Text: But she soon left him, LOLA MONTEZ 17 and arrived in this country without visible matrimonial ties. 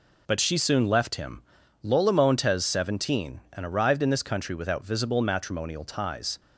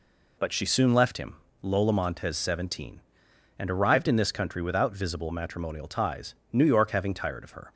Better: first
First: none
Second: goes on to say "New York having tired of her"; noticeable; from 6.5 s on; 1.2 s long

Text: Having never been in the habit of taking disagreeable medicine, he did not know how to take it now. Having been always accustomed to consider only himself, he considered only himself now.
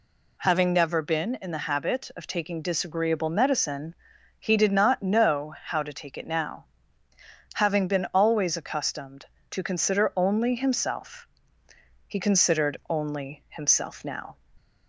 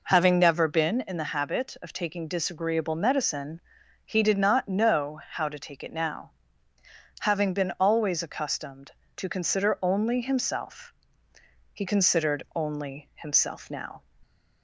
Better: first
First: none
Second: starts louder than the rest; noticeable; until 1.4 s; 4.5 dB

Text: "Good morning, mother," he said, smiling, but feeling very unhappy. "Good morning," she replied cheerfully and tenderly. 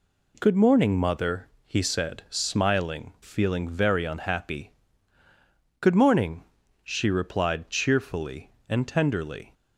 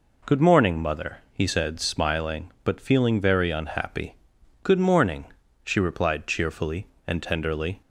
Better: second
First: skips "but"; at 3.1 s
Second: none

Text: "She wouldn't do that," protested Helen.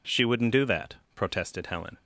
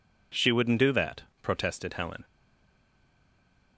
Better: first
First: none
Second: stays silent after the last word; noticeable; from 2.2 s on; 1.5 s long

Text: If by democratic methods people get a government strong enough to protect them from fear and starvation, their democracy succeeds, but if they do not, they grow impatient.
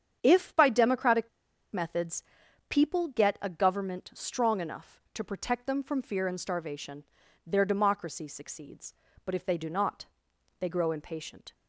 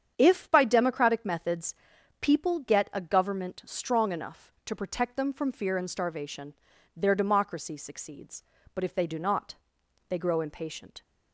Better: second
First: starts louder than the rest; strong; until 1.2 s; 8.5 dB // pauses between "democratic" and "methods"; at 1.2 s; 0.44 s long // pauses between "methods" and "people"; noticeable; at 2.2 s; 0.48 s long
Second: starts louder than the rest; strong; until 1.1 s; 8.5 dB // pauses between "methods" and "people"; noticeable; at 1.7 s; 0.48 s long

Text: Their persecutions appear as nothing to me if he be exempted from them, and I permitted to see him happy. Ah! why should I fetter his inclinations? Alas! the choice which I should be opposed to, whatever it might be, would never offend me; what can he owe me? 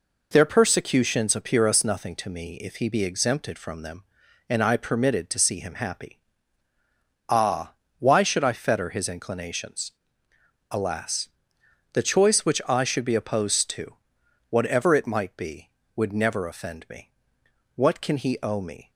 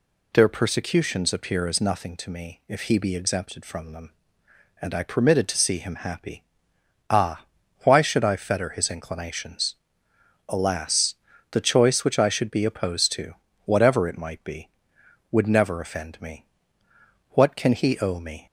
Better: second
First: says "us" for "as"; at 1.6 s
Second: none

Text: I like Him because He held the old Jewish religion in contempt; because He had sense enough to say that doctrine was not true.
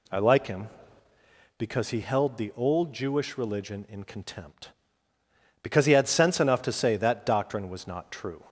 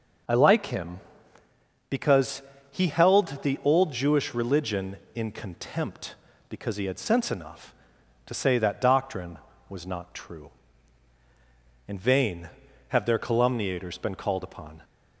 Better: first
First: none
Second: starts louder than the rest; until 2.1 s; 6 dB // pauses between "because" and "He"; slight; at 2.4 s; 0.30 s long // goes on to say "In vain have their calumniators been called upon"; strong; from 11.8 s on; 2.9 s long

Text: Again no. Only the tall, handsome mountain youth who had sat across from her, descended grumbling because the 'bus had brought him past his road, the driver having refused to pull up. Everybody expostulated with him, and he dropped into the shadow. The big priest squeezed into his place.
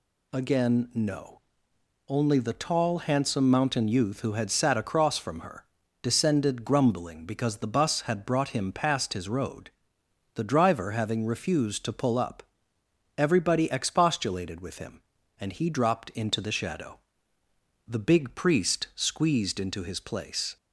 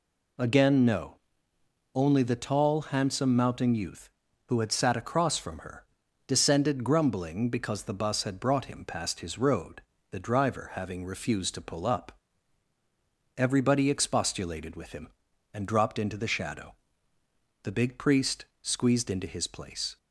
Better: first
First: none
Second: skips "he"; at 15.6 s // pauses between "priest" and "squeezed"; slight; at 18.4 s; 0.16 s long

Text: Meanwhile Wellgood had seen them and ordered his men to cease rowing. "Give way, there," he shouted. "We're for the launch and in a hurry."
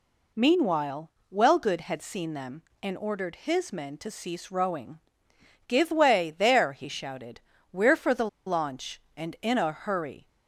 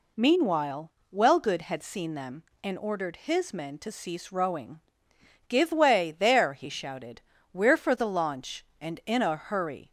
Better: second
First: pauses between "Meanwhile" and "Wellgood"; slight; at 1.1 s; 0.22 s long // pauses between "the" and "launch"; slight; at 8.2 s; 0.19 s long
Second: pauses between "Meanwhile" and "Wellgood"; slight; at 0.9 s; 0.22 s long

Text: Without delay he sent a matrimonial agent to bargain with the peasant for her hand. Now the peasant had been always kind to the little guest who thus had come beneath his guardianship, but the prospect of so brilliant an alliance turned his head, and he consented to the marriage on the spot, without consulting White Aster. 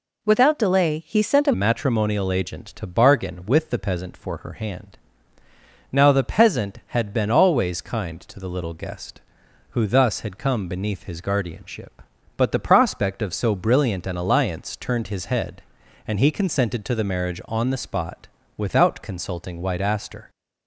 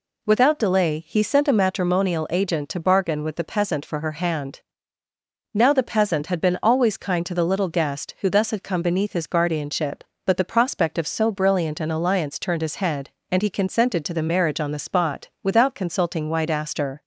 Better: second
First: changes voice at "matrimonial"; from 1.5 s on; 18.7 s long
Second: none

